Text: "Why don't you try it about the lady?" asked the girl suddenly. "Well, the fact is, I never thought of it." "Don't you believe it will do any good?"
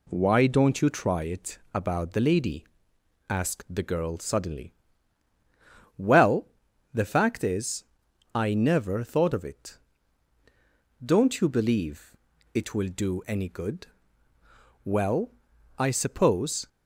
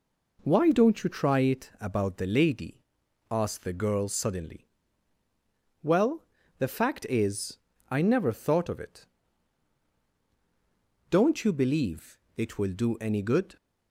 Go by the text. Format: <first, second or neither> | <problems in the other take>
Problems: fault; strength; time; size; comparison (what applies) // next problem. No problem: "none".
second | pauses between "it" and "about"; slight; at 1.5 s; 0.16 s long // pauses between "believe" and "it"; at 12.1 s; 0.38 s long; slight in the second // goes on to say "Well I suppose"; strong; from 14.8 s on; 1.8 s long